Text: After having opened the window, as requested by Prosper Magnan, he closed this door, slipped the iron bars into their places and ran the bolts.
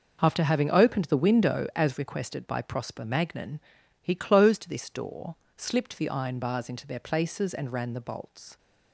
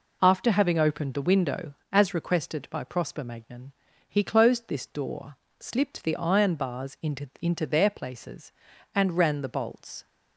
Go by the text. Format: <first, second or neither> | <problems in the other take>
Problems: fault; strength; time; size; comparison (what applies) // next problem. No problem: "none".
first | says "into" twice; at 7.4 s